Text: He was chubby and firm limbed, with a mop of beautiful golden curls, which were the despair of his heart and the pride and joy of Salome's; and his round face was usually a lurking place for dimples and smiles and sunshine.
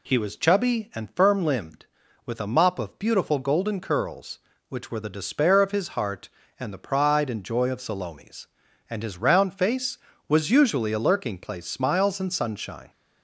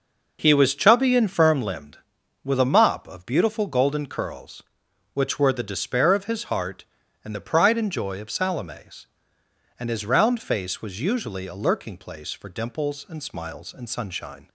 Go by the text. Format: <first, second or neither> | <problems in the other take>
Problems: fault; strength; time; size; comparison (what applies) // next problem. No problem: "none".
second | skips "for dimples and"; at 11.6 s